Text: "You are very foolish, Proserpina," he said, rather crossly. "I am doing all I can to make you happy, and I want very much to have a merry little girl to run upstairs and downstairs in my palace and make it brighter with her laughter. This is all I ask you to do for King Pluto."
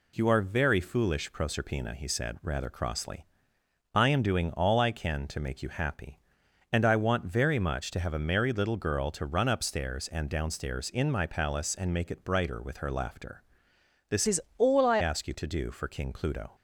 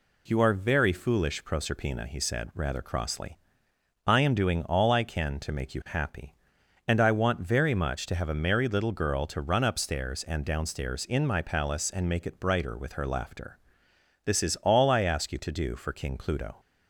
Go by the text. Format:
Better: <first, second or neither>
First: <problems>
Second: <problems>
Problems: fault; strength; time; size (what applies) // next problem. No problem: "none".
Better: second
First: changes voice from "is" to "I"; from 14.2 to 14.9 s; 0.7 s long // pauses between "is" and "all"; slight; at 14.3 s; 0.20 s long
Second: none